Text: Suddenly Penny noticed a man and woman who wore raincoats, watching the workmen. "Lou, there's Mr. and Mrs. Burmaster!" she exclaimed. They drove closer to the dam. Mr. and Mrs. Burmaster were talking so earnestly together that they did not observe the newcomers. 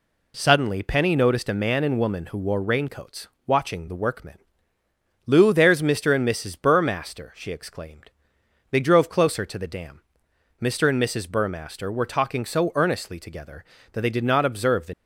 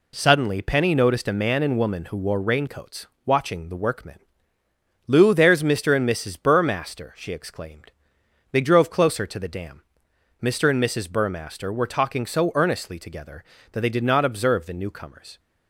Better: second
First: stops before "newcomers"; at 14.9 s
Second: none

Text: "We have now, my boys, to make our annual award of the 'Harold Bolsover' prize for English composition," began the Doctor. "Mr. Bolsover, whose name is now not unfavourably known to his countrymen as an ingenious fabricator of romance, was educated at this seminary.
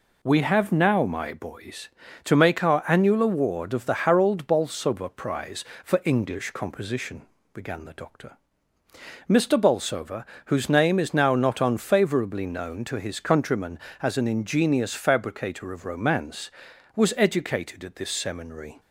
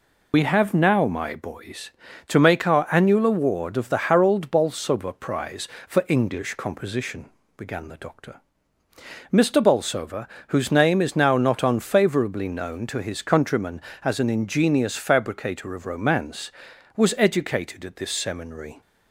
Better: first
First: none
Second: loses the start of "We"; at 0.3 s; 85 ms

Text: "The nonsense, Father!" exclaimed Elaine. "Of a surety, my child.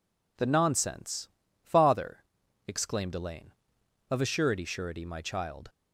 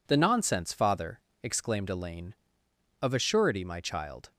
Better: second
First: says "surety" twice; at 4.6 s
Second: none

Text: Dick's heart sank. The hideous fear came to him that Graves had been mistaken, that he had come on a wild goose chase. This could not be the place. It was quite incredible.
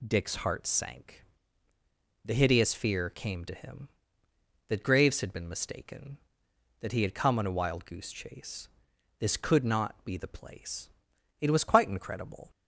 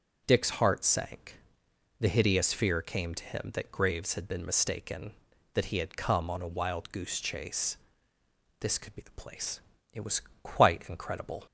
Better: first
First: none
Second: skips "not"; at 8.9 s // pauses between "was" and "quite"; slight; at 10.2 s; 0.22 s long

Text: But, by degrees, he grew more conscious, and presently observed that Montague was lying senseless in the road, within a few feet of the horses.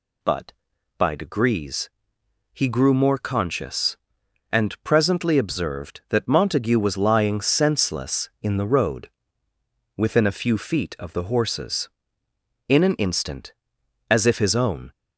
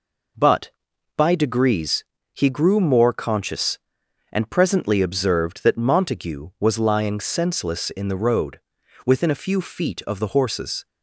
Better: second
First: goes on to say "In an instant as if his own"; strong; from 12.6 s on; 2.2 s long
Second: none

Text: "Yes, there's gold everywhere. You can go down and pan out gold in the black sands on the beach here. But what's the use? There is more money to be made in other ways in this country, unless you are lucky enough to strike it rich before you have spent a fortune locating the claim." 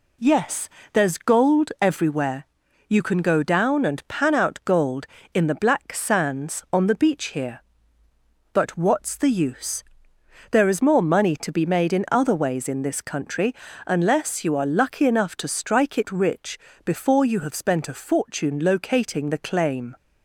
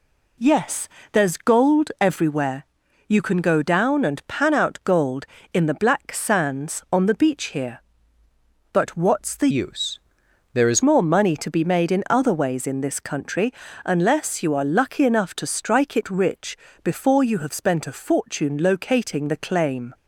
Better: first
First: pauses between "rich" and "before"; slight; at 16.5 s; 0.26 s long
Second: changes voice from "use" to "is"; from 9.4 to 10.8 s; 1.4 s long // pauses between "rich" and "before"; slight; at 16.5 s; 0.26 s long

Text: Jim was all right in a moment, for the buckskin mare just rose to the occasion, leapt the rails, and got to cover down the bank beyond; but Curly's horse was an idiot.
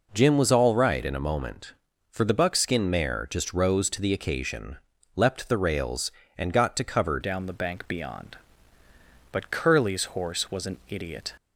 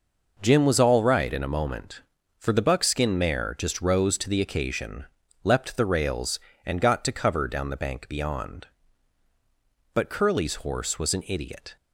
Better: second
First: changes voice at "down"; from 7.2 s on; 4.1 s long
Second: none

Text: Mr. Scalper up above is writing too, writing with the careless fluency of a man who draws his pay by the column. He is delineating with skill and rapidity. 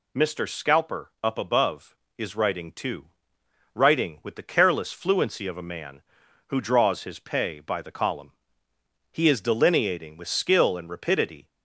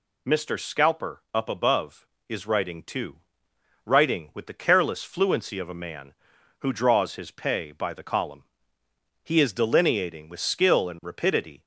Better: neither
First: none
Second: none

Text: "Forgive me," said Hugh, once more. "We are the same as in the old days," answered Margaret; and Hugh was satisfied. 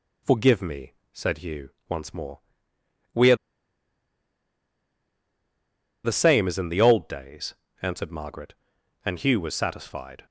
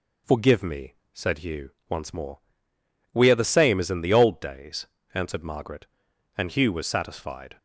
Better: second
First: pauses between "are" and "the"; strong; at 3.3 s; 2.6 s long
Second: none

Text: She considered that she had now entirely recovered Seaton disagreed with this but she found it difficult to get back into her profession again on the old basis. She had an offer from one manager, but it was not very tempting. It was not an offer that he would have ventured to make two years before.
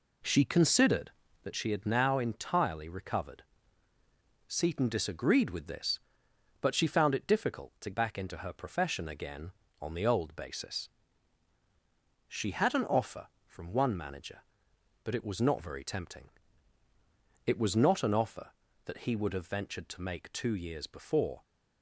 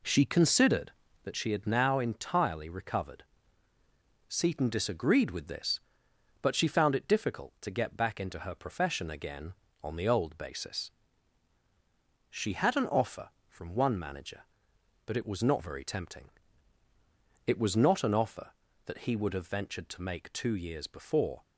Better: second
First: pauses between "recovered" and "Seaton"; at 3.4 s; 1.0 s long // skips "get"; at 7.9 s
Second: pauses between "recovered" and "Seaton"; at 3.2 s; 1.0 s long

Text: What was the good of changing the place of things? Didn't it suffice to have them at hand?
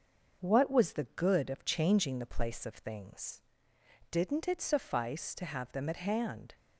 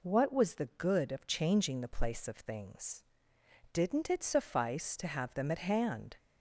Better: second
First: gets quieter; noticeable; throughout; 4 dB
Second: none

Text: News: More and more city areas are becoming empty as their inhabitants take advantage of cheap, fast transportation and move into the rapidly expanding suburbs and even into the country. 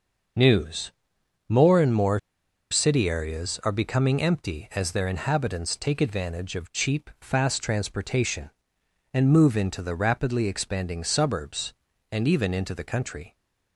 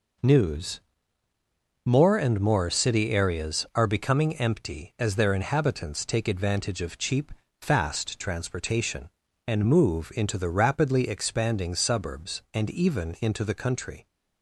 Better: second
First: pauses between "more" and "city"; noticeable; at 2.1 s; 0.52 s long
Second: none

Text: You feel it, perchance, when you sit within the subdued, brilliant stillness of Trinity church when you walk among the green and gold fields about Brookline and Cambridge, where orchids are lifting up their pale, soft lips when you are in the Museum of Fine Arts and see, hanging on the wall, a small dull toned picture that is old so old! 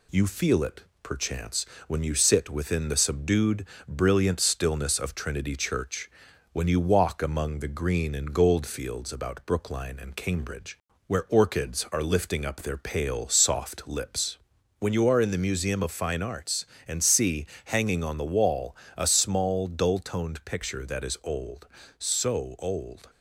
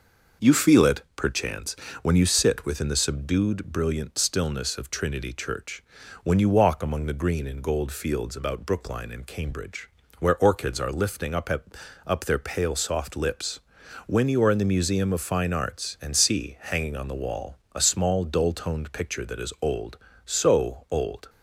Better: first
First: pauses between "church" and "when"; at 6.0 s; 0.42 s long // pauses between "lips" and "when"; at 14.3 s; 0.42 s long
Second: pauses between "church" and "when"; at 5.8 s; 0.40 s long // says "up" twice; at 12.0 s // pauses between "lips" and "when"; noticeable; at 13.5 s; 0.48 s long

